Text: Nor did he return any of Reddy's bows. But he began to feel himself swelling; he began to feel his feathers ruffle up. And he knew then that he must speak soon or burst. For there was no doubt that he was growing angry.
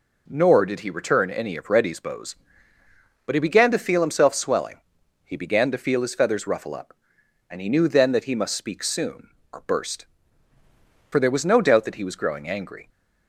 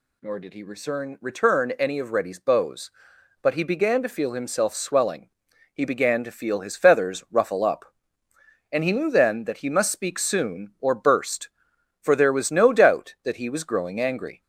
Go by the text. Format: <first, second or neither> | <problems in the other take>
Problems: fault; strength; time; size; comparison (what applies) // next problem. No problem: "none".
first | says "return" twice; at 1.2 s